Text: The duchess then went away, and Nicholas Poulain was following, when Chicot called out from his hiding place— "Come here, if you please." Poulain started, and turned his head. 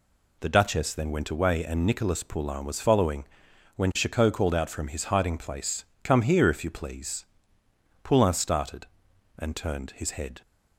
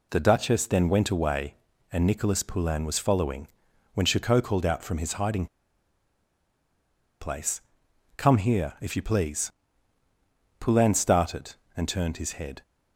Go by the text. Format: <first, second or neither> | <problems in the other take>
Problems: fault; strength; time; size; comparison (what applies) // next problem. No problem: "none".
first | pauses between "hiding" and "place"; strong; at 5.4 s; 1.7 s long